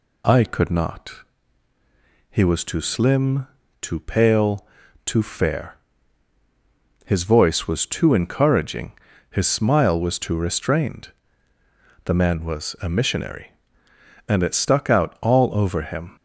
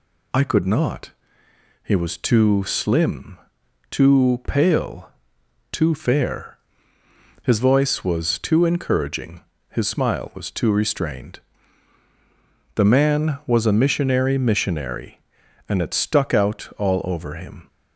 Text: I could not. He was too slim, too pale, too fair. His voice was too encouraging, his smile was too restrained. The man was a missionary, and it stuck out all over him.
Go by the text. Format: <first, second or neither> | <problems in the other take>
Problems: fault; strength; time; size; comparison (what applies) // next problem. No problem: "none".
first | says "missionary" twice; at 14.3 s